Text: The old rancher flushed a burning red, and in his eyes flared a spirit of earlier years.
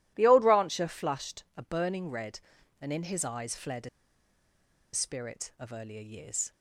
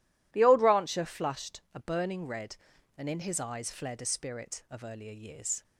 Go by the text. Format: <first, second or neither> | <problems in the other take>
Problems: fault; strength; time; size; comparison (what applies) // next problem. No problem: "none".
second | pauses between "a" and "spirit"; at 3.8 s; 1.0 s long